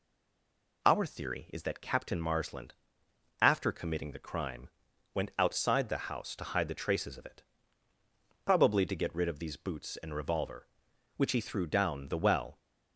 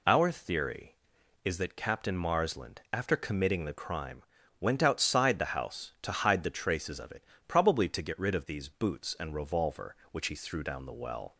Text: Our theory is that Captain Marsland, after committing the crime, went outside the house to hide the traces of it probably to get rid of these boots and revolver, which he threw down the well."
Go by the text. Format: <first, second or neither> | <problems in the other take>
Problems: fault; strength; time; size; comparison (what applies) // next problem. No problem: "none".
second | stays silent before the first word; slight; until 0.8 s; 0.8 s long // pauses between "it" and "probably"; at 7.4 s; 1.0 s long; slight in the second